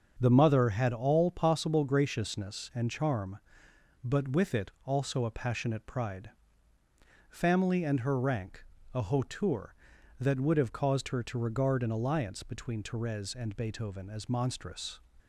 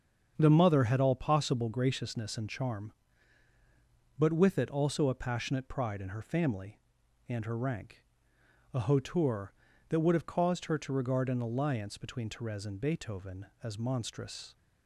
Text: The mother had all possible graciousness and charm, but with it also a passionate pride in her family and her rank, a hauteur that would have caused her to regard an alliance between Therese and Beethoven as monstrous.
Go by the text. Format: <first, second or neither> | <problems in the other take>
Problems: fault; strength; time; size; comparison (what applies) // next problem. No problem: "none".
second | starts louder than the rest; until 1.2 s; 7 dB; strong in the second // pauses between "it" and "also"; slight; at 4.6 s; 0.16 s long // skips "in her"; at 6.7 s